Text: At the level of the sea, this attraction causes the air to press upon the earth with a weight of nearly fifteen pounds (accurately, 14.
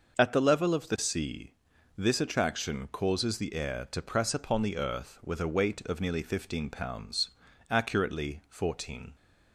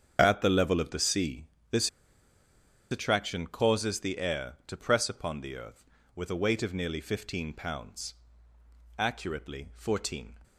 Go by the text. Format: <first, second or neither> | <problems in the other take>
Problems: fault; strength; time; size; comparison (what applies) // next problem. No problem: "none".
first | starts louder than the rest; strong; until 1.2 s; 7.5 dB // pauses between "this" and "attraction"; at 1.8 s; 1.0 s long